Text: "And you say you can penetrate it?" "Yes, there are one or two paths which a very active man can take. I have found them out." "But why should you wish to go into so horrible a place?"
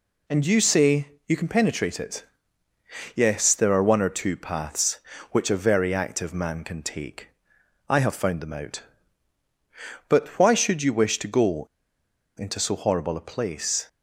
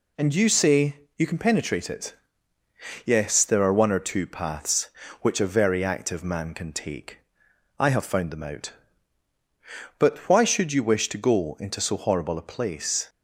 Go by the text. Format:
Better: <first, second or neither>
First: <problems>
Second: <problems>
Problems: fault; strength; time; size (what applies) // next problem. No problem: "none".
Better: second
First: pauses between "say" and "you"; slight; at 1.1 s; 0.16 s long // pauses between "go" and "into"; noticeable; at 11.6 s; 0.70 s long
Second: pauses between "say" and "you"; slight; at 0.9 s; 0.17 s long